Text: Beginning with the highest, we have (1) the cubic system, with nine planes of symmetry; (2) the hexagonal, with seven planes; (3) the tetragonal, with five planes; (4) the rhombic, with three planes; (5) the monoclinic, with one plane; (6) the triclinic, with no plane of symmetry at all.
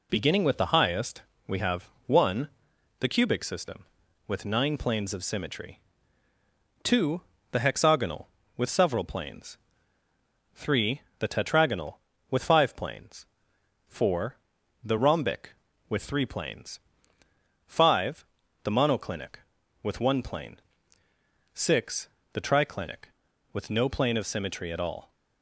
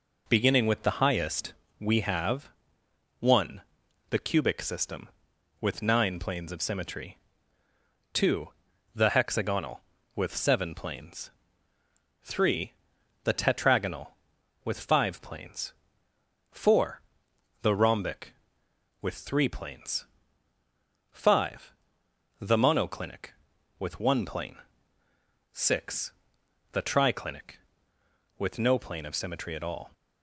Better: second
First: says "several" for "seven"; at 8.7 s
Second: none

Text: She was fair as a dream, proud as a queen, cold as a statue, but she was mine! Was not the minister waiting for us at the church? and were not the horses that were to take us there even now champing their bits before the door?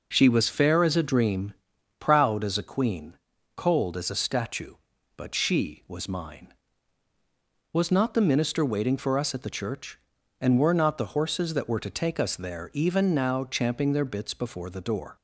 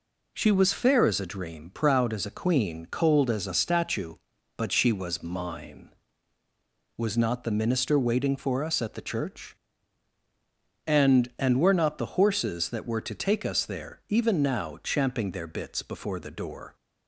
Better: first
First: none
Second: says "and" twice; at 11.3 s

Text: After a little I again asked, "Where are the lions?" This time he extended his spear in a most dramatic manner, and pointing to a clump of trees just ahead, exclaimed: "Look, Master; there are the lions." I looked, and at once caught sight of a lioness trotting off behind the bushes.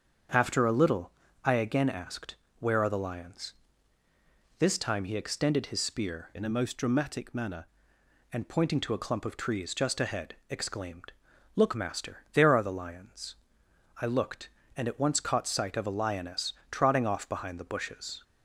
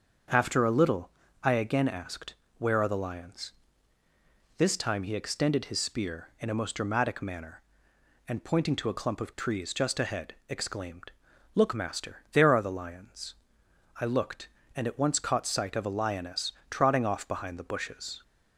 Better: second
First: starts louder than the rest; strong; until 1.6 s; 7.5 dB // pauses between "little" and "I"; slight; at 1.1 s; 0.34 s long // changes voice from "in" to "manner"; from 6.3 to 7.6 s; 1.3 s long // pauses between "lioness" and "trotting"; slight; at 16.5 s; 0.18 s long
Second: starts louder than the rest; until 1.6 s; 7 dB // pauses between "little" and "I"; slight; at 1.0 s; 0.34 s long // pauses between "lioness" and "trotting"; slight; at 16.5 s; 0.18 s long

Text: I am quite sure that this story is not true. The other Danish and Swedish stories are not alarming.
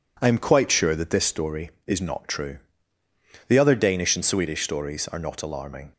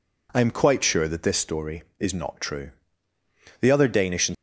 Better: first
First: none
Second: stops before "Swedish stories are not alarming"; at 4.3 s

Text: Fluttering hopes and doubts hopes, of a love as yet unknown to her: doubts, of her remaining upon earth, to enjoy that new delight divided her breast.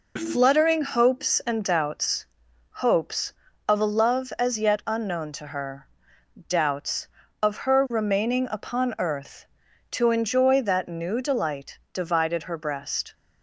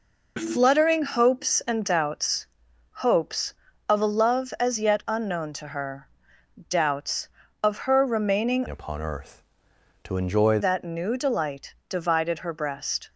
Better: first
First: pauses between "doubts" and "hopes"; noticeable; at 2.2 s; 0.46 s long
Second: pauses between "doubts" and "hopes"; noticeable; at 2.4 s; 0.46 s long // changes voice from "upon" to "enjoy"; from 8.6 to 10.5 s; 1.9 s long

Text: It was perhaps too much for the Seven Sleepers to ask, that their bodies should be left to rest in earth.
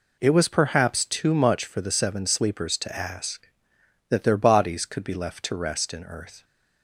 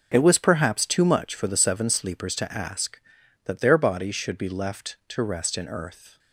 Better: second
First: says "could" for "should"; at 4.8 s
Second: none

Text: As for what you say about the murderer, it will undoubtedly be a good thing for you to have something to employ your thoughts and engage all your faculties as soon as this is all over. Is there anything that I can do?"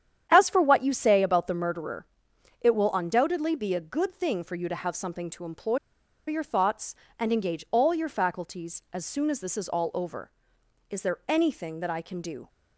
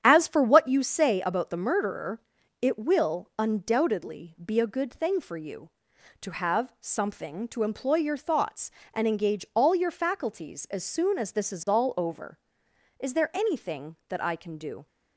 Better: second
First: starts louder than the rest; strong; until 1.3 s; 9.5 dB // pauses between "employ" and "your"; noticeable; at 5.7 s; 0.50 s long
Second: starts louder than the rest; strong; until 1.0 s; 9.5 dB

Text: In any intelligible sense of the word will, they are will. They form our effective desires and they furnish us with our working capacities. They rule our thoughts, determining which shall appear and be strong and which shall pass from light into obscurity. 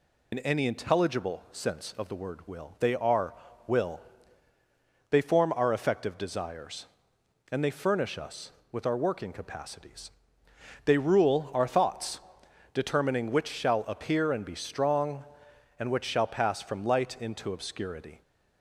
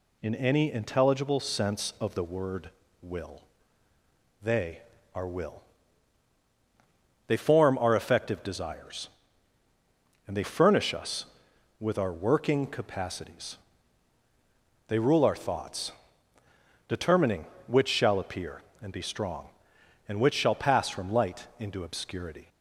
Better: second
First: loses the start of "In"; at 0.3 s; 50 ms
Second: none

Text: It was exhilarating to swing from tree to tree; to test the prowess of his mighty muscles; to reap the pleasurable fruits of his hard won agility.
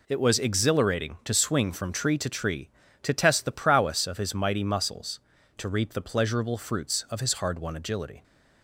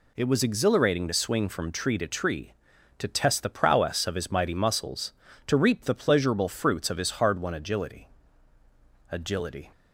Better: first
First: none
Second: says "agility" twice; at 9.1 s

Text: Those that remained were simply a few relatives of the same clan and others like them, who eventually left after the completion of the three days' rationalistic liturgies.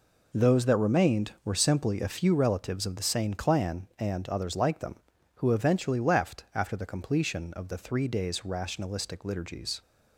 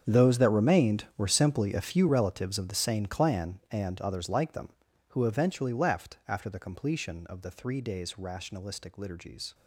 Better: first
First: none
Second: gets quieter; strong; throughout; 16.5 dB

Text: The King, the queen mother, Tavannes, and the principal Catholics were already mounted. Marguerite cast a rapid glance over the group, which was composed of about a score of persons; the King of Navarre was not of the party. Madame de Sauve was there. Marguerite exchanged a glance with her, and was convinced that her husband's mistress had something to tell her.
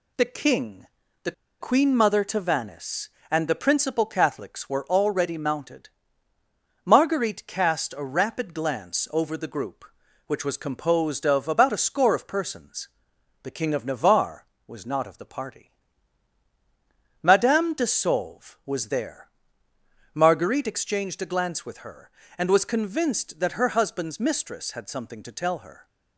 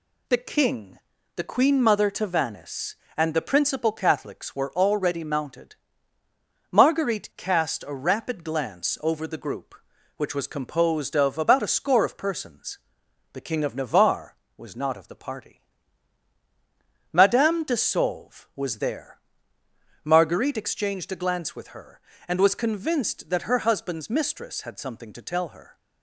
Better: second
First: pauses between "the" and "queen"; slight; at 1.3 s; 0.28 s long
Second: none

